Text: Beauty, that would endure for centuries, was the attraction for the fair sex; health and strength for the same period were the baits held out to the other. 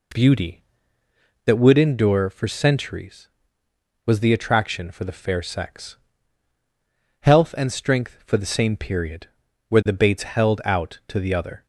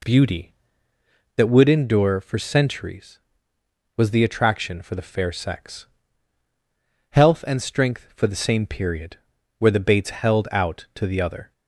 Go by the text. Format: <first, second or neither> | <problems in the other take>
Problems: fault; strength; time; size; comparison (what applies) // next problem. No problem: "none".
neither | none